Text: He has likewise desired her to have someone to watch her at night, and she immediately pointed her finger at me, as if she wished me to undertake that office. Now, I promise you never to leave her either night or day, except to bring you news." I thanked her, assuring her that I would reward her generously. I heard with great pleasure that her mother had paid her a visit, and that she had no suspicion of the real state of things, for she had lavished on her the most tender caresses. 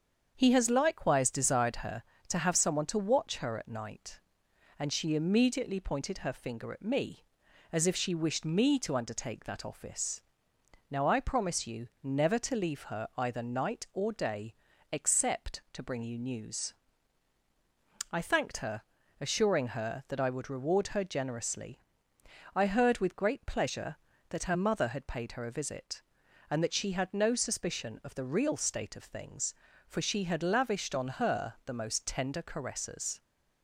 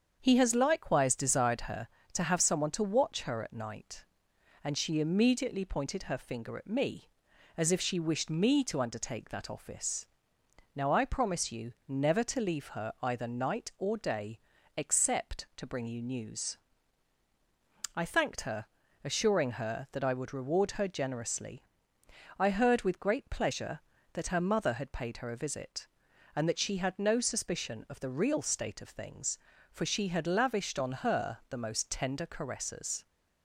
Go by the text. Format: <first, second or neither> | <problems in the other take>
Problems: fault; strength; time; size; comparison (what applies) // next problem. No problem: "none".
neither | starts louder than the rest; strong; the same in both